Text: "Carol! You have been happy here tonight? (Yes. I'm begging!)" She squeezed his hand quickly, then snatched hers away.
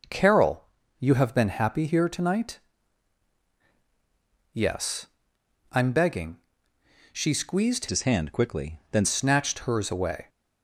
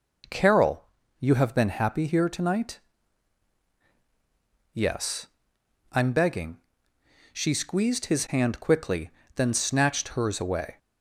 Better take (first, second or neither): second